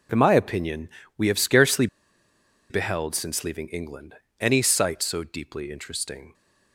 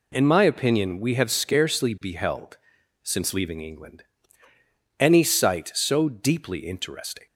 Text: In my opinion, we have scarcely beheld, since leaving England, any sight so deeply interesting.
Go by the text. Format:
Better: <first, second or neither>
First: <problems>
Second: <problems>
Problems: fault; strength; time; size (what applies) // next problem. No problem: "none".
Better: second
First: pauses between "scarcely" and "beheld"; noticeable; at 1.8 s; 0.83 s long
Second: none